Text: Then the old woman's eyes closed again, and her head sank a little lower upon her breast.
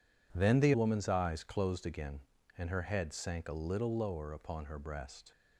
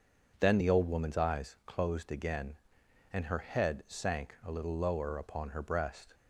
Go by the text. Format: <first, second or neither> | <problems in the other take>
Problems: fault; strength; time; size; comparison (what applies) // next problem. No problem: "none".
second | skips "old"; at 0.7 s